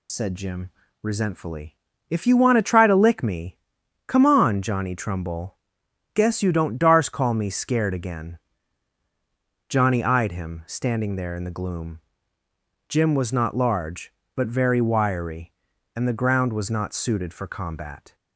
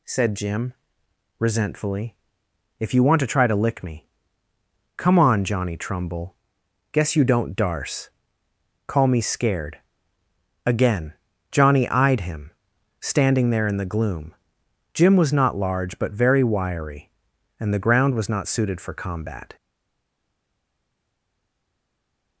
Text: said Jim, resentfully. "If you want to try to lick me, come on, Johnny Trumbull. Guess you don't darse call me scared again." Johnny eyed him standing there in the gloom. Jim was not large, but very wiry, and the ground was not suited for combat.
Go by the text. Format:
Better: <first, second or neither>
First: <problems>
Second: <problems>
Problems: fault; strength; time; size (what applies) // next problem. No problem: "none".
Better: first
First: none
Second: pauses between "darse" and "call"; noticeable; at 8.0 s; 0.76 s long // pauses between "scared" and "again"; noticeable; at 9.7 s; 0.86 s long // pauses between "him" and "standing"; noticeable; at 12.4 s; 0.50 s long // stays silent after the last word; strong; from 19.5 s on; 2.9 s long